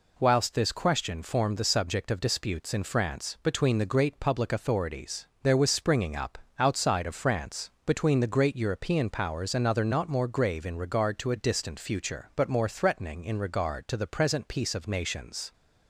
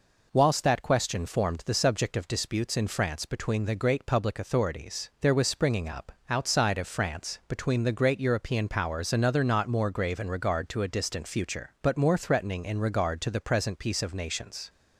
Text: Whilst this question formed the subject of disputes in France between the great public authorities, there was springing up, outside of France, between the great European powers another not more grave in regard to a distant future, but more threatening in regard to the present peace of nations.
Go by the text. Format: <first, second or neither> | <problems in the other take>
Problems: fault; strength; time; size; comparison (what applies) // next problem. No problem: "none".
first | says "that" for "this"; at 0.6 s